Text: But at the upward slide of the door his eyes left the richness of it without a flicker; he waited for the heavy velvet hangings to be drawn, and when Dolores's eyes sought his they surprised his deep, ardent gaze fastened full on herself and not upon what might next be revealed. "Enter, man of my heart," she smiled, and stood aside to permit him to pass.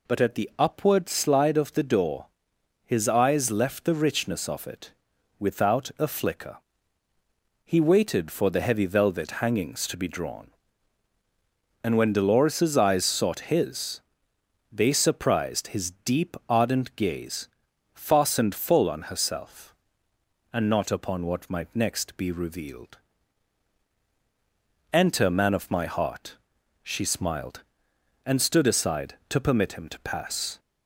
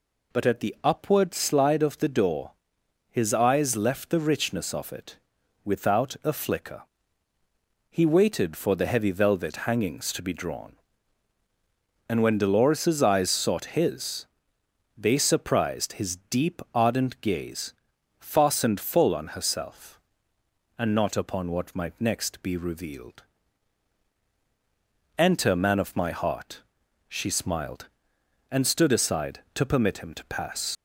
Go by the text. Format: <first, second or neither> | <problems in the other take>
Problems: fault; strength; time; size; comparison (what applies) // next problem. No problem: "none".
first | pauses between "door" and "his"; noticeable; at 2.5 s; 0.58 s long; noticeable in the first // pauses between "it" and "without"; noticeable; at 5.1 s; 0.48 s long; noticeable in the first // pauses between "his" and "they"; noticeable; at 14.2 s; 0.74 s long; noticeable in the first // pauses between "gaze" and "fastened"; noticeable; at 17.7 s; 0.46 s long; noticeable in the first // leaves "pass" unfinished; at 30.7 s; 95 ms